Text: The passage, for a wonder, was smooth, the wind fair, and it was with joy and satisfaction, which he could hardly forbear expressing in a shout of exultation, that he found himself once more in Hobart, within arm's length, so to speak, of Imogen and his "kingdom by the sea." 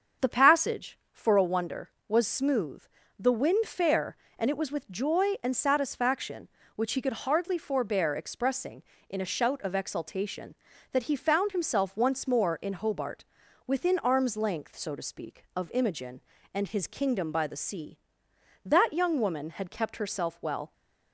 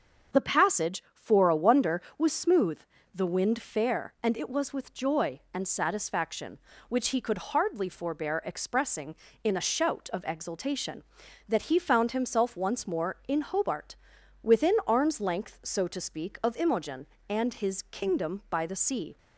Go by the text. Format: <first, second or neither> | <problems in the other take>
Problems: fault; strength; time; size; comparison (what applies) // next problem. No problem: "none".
second | starts louder than the rest; until 1.3 s; 7 dB; also in the second // goes on to say "That young woman had kept herself well"; strong; from 18.6 s on; 2.0 s long